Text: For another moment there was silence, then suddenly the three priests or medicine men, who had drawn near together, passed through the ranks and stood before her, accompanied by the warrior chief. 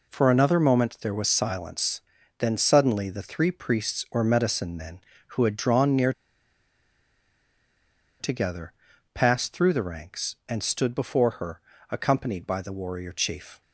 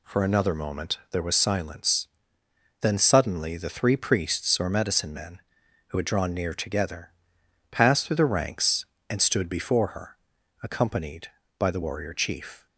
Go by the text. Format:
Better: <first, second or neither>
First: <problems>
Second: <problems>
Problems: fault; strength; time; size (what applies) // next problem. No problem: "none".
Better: second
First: pauses between "near" and "together"; strong; at 6.1 s; 2.0 s long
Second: none